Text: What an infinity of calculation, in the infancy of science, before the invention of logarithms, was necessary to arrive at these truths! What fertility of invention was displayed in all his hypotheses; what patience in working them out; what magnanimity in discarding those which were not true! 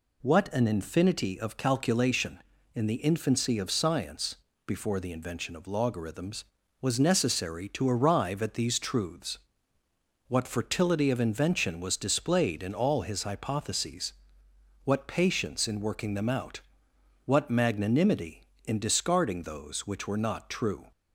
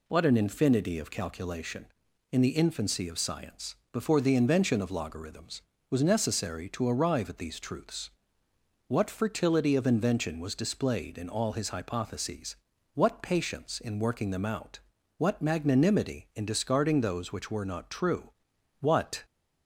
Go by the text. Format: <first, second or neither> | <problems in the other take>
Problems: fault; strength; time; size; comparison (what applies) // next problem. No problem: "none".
first | goes on to say "What"; slight; from 18.7 s on; 0.44 s long